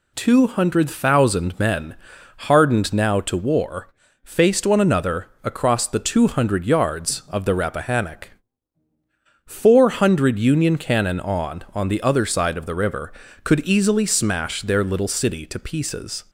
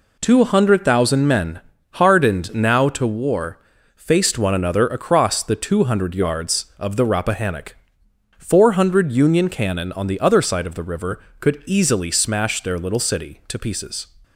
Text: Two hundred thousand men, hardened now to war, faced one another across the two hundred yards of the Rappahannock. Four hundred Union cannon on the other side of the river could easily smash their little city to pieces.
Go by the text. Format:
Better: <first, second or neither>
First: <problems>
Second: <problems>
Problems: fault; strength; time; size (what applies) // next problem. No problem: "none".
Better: second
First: pauses between "another" and "across"; slight; at 5.2 s; 0.16 s long // says "on" twice; at 11.7 s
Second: none